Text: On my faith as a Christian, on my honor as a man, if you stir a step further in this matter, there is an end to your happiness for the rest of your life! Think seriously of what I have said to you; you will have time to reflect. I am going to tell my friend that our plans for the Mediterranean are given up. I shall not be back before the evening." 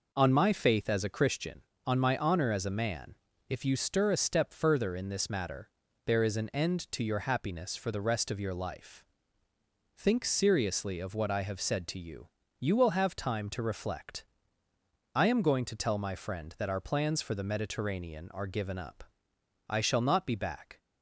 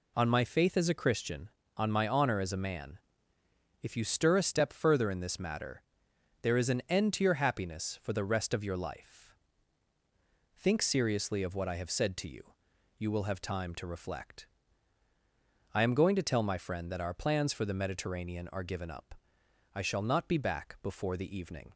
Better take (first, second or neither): second